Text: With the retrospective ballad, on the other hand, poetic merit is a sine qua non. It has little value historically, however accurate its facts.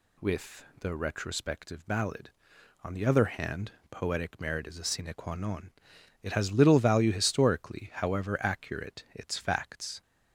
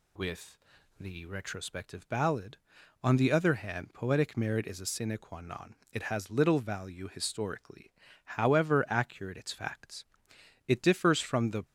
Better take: first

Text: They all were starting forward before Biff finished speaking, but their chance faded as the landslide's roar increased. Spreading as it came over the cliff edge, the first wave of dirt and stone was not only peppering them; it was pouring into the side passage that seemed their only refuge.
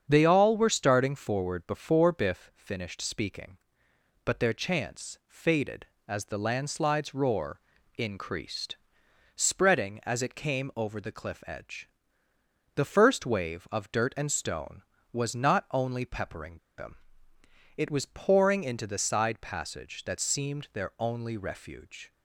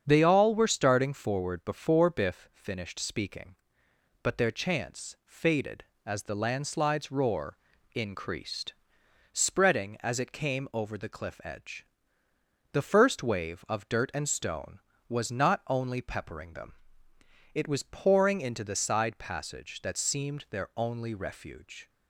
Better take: second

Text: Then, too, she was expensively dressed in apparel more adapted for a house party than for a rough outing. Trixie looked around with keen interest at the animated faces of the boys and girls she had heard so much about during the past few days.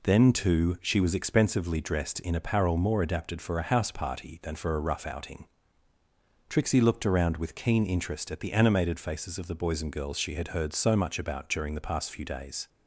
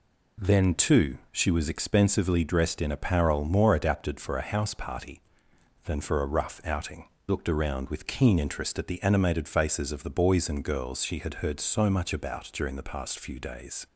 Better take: first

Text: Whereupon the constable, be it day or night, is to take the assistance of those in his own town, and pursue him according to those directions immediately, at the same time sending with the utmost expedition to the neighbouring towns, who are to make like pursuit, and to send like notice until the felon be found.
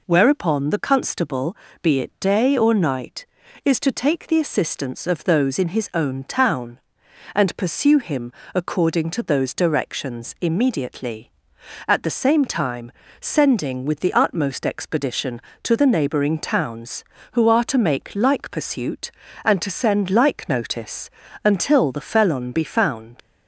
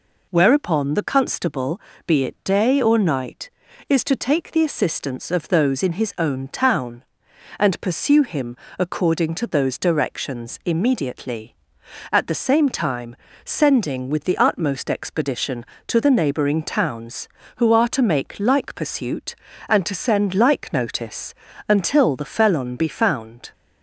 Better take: second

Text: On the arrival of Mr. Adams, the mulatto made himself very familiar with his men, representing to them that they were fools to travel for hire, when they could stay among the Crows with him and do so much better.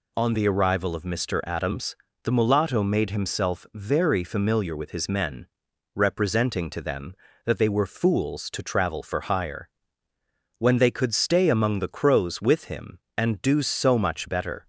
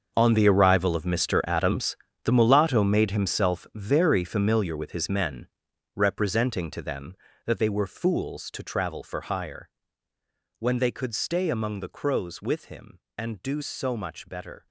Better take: first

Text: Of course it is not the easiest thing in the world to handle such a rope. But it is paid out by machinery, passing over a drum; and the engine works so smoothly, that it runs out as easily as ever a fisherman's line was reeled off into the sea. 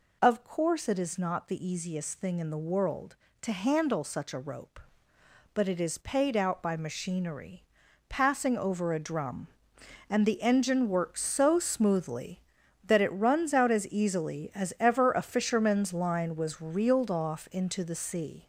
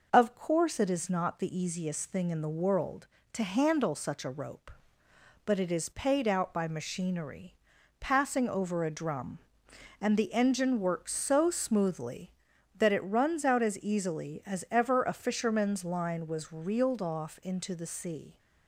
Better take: second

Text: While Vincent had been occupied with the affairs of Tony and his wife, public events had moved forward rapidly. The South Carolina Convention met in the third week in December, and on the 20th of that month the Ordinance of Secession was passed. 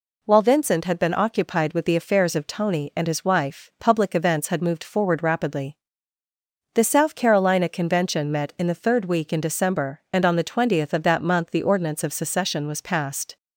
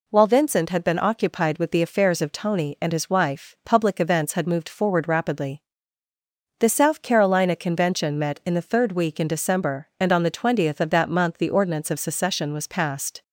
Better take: neither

